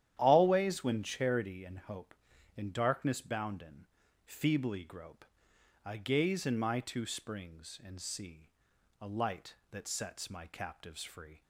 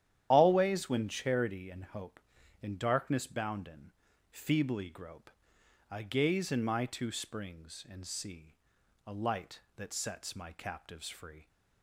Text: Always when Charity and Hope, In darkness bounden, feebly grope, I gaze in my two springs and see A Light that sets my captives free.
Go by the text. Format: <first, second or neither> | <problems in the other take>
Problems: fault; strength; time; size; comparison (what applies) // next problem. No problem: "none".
first | loses the start of "Always"; at 0.3 s; 60 ms // starts louder than the rest; strong; until 1.3 s; 11 dB; strong in the first // pauses between "see" and "A"; noticeable; at 8.5 s; 0.50 s long; noticeable in the first